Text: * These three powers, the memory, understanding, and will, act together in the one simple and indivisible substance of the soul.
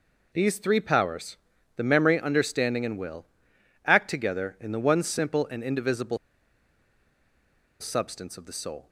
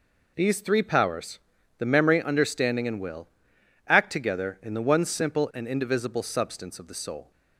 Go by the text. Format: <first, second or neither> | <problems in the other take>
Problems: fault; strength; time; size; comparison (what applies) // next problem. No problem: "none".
second | pauses between "indivisible" and "substance"; strong; at 6.1 s; 1.6 s long